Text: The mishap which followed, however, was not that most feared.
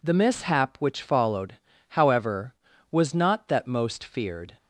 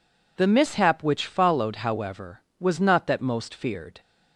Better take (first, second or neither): neither